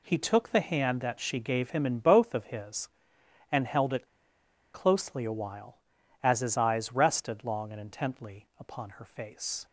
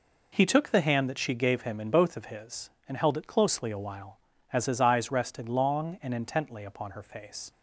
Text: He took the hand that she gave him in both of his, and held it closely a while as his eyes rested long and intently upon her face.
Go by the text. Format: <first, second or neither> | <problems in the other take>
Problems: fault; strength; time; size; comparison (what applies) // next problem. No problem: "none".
second | pauses between "it" and "closely"; noticeable; at 4.0 s; 0.69 s long